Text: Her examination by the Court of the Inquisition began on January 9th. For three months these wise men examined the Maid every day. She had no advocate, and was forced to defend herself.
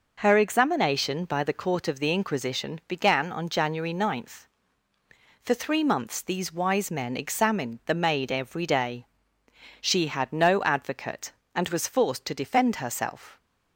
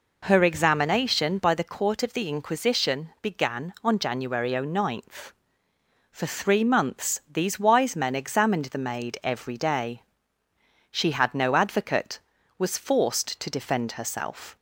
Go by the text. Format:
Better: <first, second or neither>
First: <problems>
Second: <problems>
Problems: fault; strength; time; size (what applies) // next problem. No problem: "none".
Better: first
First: none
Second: skips "and"; at 12.3 s